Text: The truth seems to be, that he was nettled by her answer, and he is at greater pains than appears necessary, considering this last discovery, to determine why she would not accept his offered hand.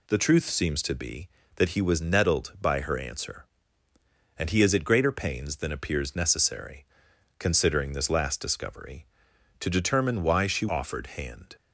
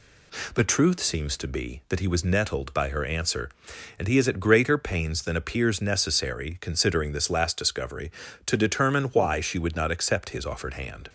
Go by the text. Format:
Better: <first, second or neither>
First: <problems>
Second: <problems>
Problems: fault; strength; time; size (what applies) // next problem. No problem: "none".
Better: second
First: skips "would not accept his"; at 10.6 s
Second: none